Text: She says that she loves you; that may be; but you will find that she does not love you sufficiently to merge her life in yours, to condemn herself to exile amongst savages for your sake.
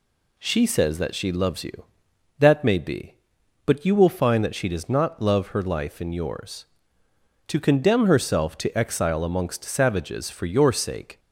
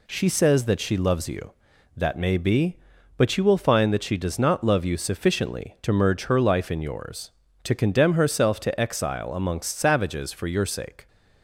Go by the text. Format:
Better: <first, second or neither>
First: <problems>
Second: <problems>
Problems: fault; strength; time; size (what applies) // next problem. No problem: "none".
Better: second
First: skips "you sufficiently to merge"; at 5.4 s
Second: none